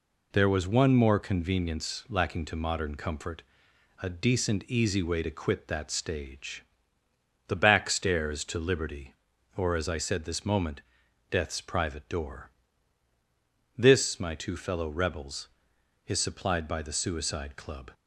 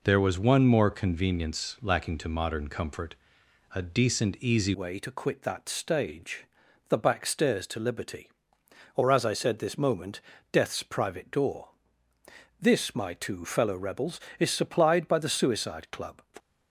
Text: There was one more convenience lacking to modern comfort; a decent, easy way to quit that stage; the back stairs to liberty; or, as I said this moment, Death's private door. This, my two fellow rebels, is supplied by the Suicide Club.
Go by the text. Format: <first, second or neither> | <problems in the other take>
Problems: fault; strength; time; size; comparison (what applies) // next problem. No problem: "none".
first | changes voice at "way"; from 4.7 s on; 11.5 s long